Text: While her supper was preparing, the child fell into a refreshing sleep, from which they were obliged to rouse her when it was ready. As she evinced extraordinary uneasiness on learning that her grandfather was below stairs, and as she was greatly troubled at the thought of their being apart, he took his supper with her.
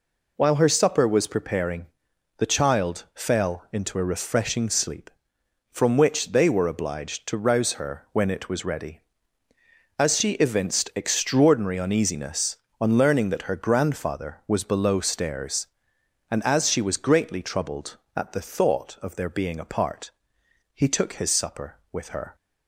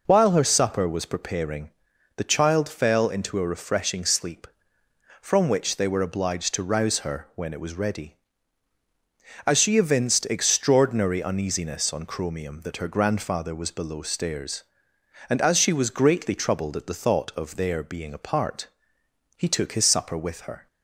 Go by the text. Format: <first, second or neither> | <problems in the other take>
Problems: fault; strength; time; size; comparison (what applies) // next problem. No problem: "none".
first | says "chromium" for "learning"; at 12.0 s